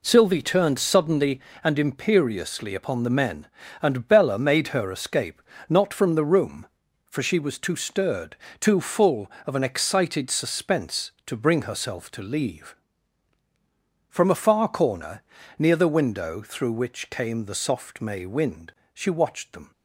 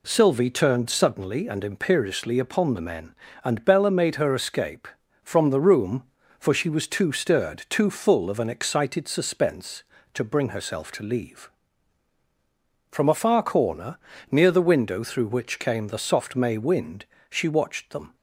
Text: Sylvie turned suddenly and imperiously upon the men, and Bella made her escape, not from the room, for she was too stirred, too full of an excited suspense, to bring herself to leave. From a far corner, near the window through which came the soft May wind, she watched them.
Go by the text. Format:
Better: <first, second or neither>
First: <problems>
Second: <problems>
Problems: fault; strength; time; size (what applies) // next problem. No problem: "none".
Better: first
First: none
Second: skips "not"; at 5.0 s